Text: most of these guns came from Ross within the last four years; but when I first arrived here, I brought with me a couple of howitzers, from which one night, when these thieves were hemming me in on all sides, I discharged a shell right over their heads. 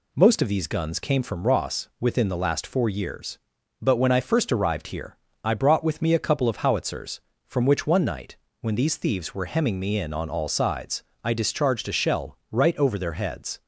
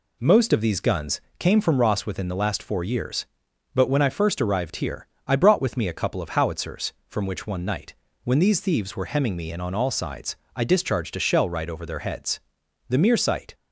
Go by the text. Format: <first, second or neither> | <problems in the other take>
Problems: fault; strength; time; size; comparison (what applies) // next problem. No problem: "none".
first | pauses between "guns" and "came"; slight; at 1.1 s; 0.18 s long // goes on to say "The mere sight"; noticeable; from 12.8 s on; 0.66 s long